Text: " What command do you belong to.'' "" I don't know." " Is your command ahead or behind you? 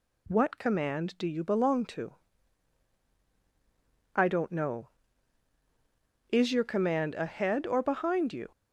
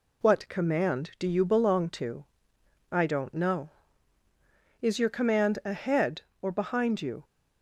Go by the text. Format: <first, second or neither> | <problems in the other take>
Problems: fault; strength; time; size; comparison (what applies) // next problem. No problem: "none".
neither | none